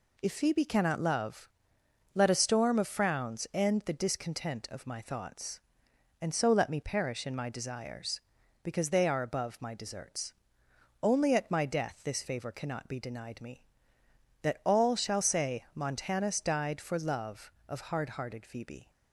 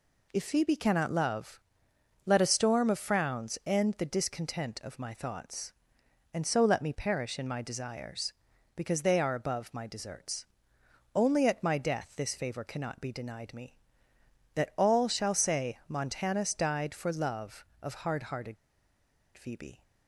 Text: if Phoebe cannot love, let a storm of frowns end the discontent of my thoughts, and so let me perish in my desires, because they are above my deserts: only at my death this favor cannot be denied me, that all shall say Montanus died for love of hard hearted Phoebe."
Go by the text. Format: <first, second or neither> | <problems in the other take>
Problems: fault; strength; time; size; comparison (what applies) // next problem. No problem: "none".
first | pauses between "hearted" and "Phoebe"; noticeable; at 18.5 s; 0.81 s long